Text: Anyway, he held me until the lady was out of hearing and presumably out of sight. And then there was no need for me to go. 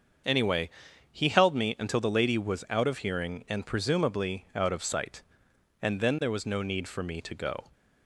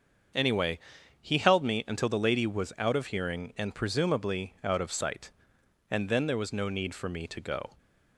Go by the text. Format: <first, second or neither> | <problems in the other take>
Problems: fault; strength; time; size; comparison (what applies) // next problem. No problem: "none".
neither | starts louder than the rest; the same in both